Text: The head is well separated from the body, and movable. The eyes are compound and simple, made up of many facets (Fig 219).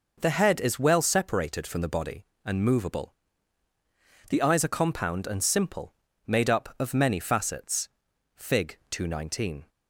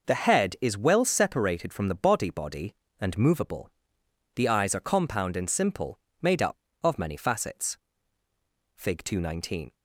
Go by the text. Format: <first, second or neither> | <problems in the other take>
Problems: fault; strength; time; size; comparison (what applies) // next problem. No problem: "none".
first | says "body" twice; at 2.2 s